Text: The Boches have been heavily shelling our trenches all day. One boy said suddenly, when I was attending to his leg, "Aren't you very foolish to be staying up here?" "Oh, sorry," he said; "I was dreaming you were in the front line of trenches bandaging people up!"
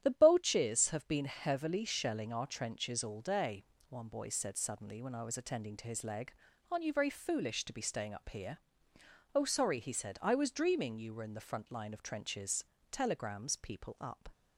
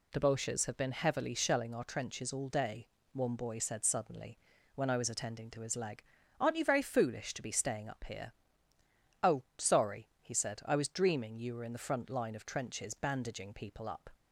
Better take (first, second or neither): second